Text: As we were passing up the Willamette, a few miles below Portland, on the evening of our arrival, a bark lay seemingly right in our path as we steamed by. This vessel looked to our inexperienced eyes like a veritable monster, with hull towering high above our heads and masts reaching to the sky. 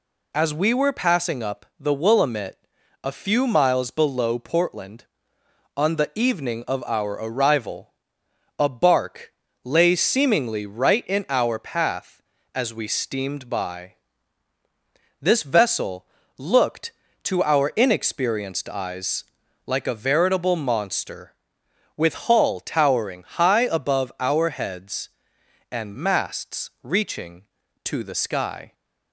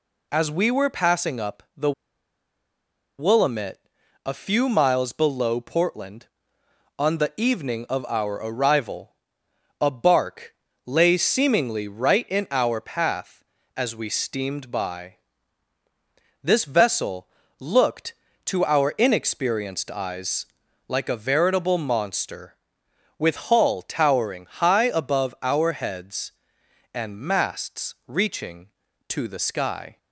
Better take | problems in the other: first | pauses between "the" and "Willamette"; strong; at 1.9 s; 1.2 s long // pauses between "bark" and "lay"; slight; at 10.5 s; 0.32 s long; slight in the first // pauses between "vessel" and "looked"; slight; at 17.2 s; 0.32 s long; slight in the first // pauses between "eyes" and "like"; at 20.4 s; 0.42 s long; also in the first

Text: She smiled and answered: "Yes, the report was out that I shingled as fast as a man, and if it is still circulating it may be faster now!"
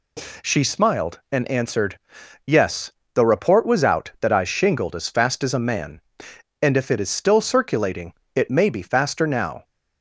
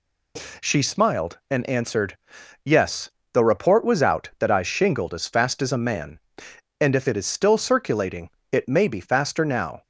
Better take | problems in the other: neither | pauses between "circulating" and "it"; slight; the same in both

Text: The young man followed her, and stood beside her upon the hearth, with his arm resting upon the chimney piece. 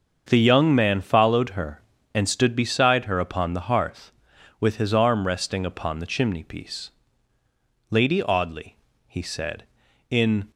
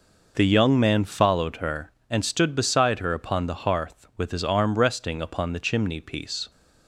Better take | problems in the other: second | starts louder than the rest; until 1.2 s; 6.5 dB // goes on to say "Lady Audley he said in"; strong; from 7.8 s on; 2.6 s long

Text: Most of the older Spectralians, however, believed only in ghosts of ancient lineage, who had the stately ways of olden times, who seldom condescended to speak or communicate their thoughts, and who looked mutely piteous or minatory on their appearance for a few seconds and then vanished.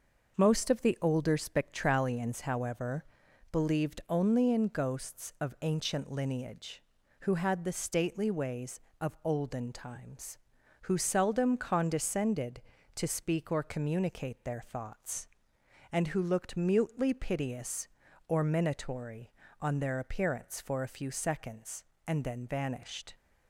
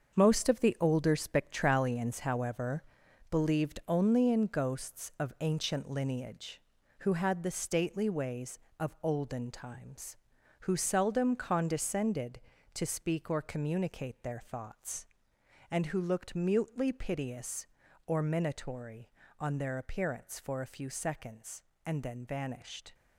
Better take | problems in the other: first | gets quieter; strong; throughout; 9 dB

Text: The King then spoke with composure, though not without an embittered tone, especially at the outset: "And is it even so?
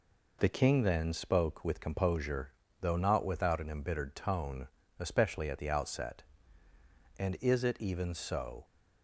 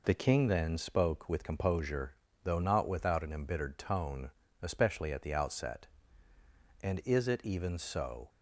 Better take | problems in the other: neither | none

